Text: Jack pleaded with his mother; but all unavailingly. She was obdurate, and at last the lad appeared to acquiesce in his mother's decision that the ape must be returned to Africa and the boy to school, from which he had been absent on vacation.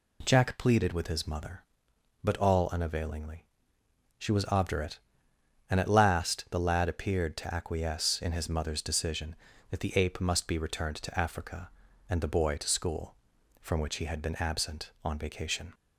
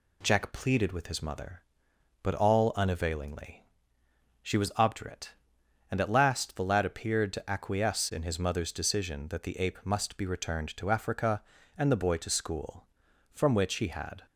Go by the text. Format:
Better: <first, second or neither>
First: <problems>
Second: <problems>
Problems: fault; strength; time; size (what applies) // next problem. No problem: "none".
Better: first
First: none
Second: stops before "been absent on vacation"; at 14.2 s